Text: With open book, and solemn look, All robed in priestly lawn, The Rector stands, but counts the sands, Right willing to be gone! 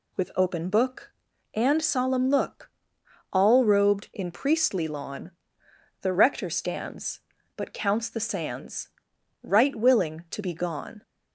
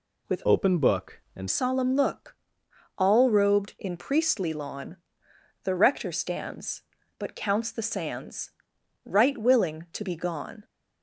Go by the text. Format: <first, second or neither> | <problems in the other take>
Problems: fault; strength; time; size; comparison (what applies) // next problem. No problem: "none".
first | changes voice from "open" to "and"; from 0.4 to 1.4 s; 1.0 s long